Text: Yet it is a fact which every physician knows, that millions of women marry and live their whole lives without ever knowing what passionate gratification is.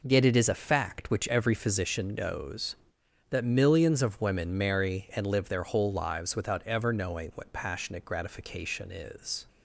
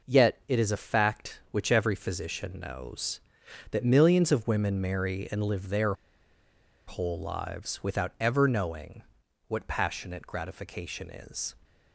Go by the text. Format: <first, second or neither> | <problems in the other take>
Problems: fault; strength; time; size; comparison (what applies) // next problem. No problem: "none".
first | pauses between "their" and "whole"; noticeable; at 5.9 s; 0.92 s long // pauses between "knowing" and "what"; noticeable; at 9.0 s; 0.46 s long